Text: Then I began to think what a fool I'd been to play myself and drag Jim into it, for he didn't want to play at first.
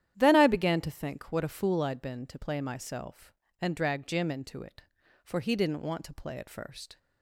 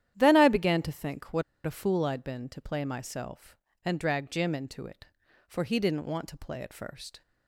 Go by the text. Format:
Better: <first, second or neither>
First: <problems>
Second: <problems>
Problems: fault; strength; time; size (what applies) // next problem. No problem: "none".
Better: first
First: starts louder than the rest; strong; until 1.1 s; 10.5 dB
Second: starts louder than the rest; strong; until 1.1 s; 11 dB // pauses between "what" and "a"; slight; at 1.4 s; 0.22 s long